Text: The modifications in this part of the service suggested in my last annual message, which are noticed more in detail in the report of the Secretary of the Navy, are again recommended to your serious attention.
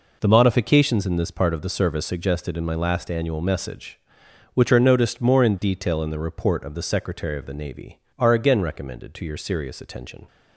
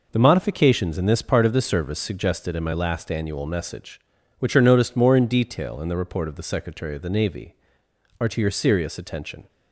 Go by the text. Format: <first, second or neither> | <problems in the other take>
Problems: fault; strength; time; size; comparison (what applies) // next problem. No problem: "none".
first | skips "again recommended"; at 8.2 s